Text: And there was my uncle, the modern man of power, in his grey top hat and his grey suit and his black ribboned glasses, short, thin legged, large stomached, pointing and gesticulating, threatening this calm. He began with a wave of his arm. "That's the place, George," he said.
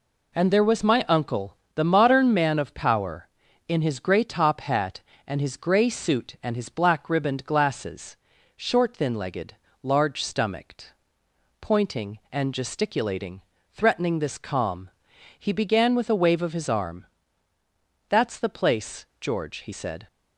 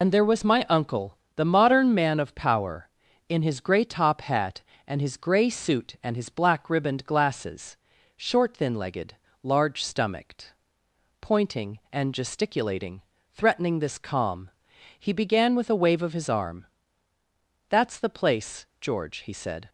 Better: first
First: none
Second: loses the start of "And"; at 0.0 s; 55 ms

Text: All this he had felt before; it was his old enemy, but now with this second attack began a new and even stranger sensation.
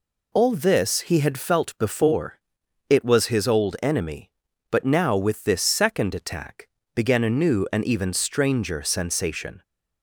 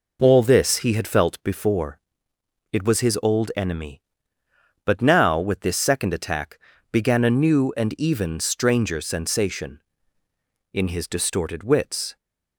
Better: first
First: pauses between "attack" and "began"; slight; at 6.6 s; 0.26 s long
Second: pauses between "attack" and "began"; slight; at 6.5 s; 0.32 s long // goes on to say "In his distorted wits"; from 10.7 s on; 1.4 s long

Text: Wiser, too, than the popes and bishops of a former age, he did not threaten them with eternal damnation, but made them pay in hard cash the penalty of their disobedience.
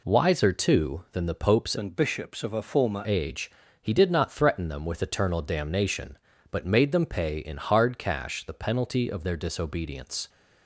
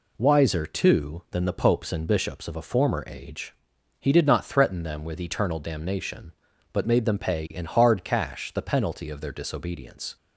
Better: second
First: changes voice from "and" to "former"; from 1.7 to 3.0 s; 1.3 s long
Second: none

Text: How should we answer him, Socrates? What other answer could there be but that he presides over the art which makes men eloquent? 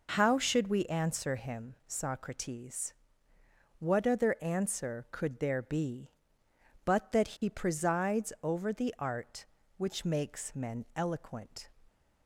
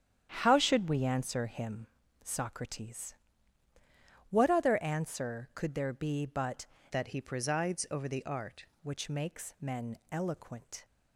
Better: first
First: none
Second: starts louder than the rest; strong; until 1.3 s; 9.5 dB // changes voice from "that" to "art"; from 6.9 to 8.6 s; 1.7 s long // pauses between "men" and "eloquent"; slight; at 9.9 s; 0.16 s long

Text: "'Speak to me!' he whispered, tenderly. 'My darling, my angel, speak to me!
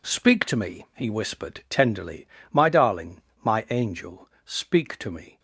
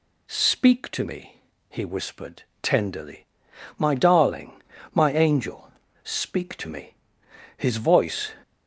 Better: first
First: none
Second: goes on to say "His voice"; noticeable; from 7.5 s on; 0.76 s long

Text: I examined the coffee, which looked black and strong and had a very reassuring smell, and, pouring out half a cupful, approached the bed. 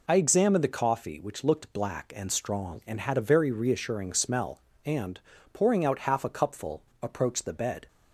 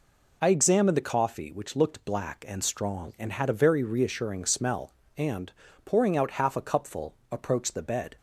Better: neither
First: none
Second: none

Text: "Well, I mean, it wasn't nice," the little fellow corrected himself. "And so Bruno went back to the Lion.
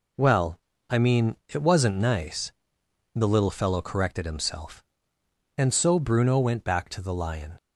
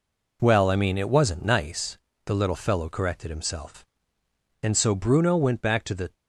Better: first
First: none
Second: stops before "Lion"; at 6.1 s

